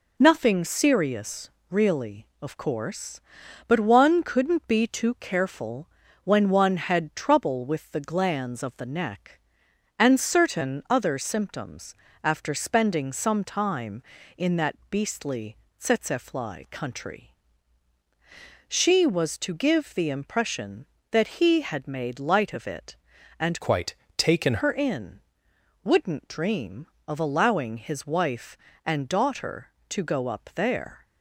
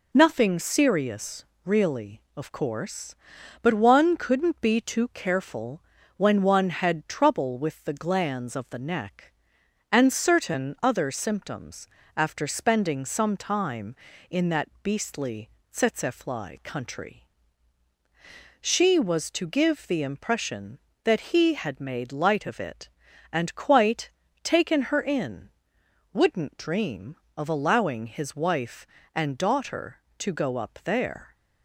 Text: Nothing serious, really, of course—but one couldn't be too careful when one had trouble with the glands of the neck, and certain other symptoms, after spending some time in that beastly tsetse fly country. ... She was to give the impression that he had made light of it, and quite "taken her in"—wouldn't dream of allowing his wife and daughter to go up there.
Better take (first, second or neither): second